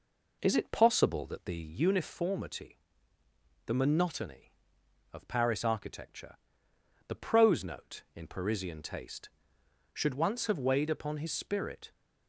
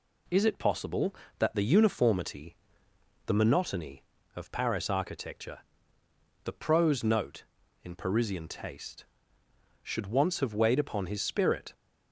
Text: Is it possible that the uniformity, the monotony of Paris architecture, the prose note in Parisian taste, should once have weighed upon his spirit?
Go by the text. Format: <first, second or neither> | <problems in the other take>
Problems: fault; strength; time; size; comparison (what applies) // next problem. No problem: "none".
second | starts louder than the rest; noticeable; until 1.9 s; 4.5 dB